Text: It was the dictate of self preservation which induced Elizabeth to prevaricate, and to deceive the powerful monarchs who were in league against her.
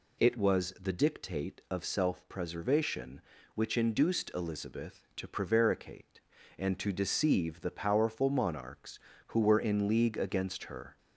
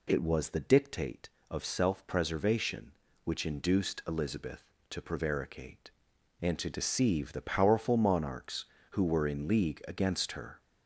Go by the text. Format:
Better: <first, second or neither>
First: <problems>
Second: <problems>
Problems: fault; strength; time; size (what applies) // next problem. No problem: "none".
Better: neither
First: none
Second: none